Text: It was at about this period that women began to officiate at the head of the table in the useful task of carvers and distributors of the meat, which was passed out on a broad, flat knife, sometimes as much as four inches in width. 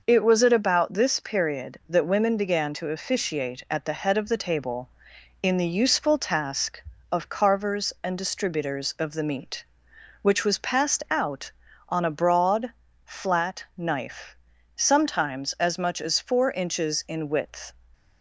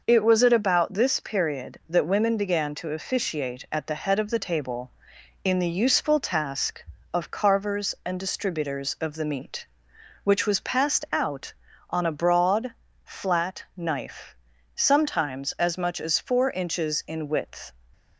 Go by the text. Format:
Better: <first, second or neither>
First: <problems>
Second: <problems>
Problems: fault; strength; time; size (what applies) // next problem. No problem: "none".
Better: neither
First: none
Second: none